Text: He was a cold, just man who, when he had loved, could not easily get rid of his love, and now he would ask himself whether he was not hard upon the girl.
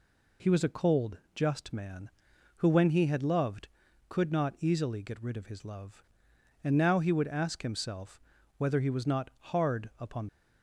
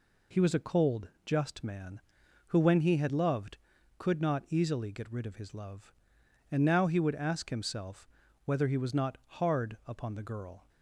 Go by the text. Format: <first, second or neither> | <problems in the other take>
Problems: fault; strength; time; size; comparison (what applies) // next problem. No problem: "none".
second | pauses between "himself" and "whether"; at 8.1 s; 0.38 s long; also in the second // stops before "the girl"; at 10.2 s